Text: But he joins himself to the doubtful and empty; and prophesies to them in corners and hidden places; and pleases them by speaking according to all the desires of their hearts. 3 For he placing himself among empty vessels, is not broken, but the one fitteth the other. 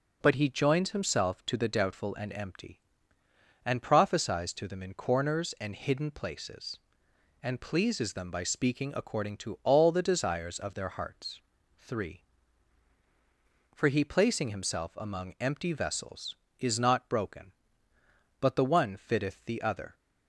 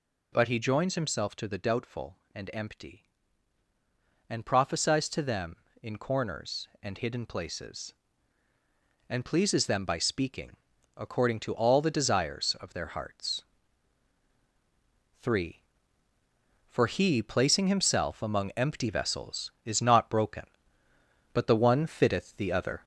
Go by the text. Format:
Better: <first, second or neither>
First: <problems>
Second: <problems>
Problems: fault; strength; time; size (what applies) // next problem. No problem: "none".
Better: first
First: none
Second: gets louder; throughout; 3.5 dB // pauses between "speaking" and "according"; at 10.5 s; 0.42 s long